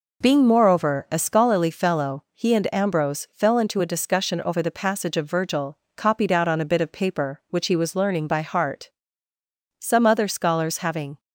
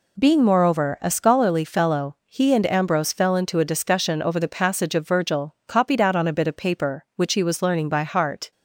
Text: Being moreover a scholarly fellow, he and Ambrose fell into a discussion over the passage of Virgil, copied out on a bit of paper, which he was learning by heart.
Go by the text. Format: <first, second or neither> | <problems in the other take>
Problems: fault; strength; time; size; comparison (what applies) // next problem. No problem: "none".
second | goes on to say "Some other scholars having"; from 9.7 s on; 1.4 s long